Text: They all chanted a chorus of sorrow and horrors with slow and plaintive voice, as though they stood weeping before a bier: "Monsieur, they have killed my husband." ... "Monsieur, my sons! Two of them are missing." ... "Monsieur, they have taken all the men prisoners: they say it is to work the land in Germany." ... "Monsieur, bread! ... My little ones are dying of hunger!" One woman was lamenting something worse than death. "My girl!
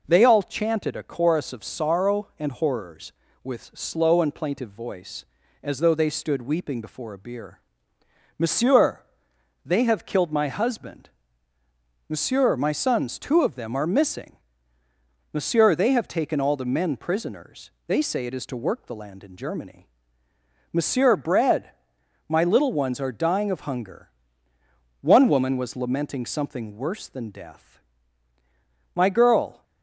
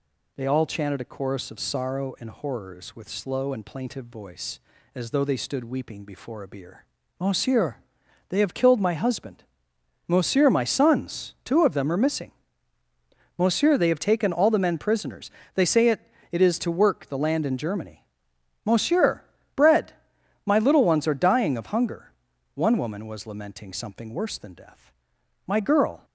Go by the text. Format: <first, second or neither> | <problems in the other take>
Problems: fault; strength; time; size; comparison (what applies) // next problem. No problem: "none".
first | says "it" twice; at 16.3 s